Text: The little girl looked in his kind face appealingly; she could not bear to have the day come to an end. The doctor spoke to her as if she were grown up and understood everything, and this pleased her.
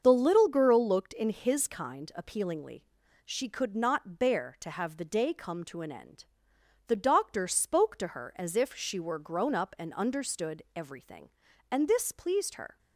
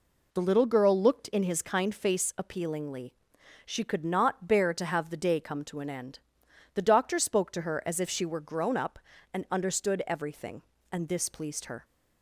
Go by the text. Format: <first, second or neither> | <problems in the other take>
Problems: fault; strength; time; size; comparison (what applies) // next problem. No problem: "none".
second | starts louder than the rest; until 1.0 s; 6.5 dB // skips "face"; at 2.1 s